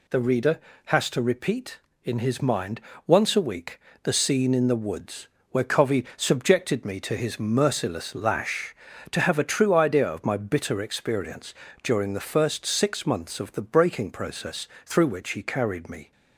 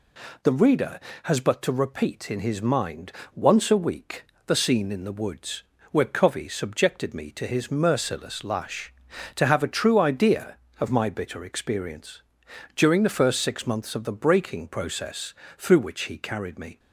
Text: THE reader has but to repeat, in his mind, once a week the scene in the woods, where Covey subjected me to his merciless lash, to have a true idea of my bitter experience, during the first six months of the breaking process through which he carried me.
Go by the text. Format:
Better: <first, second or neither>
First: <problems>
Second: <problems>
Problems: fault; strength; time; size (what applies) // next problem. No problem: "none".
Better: second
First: skips "but"; at 1.1 s // pauses between "week" and "the"; slight; at 3.7 s; 0.26 s long // pauses between "process" and "through"; slight; at 14.6 s; 0.16 s long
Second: pauses between "week" and "the"; slight; at 4.2 s; 0.22 s long // pauses between "process" and "through"; slight; at 15.3 s; 0.24 s long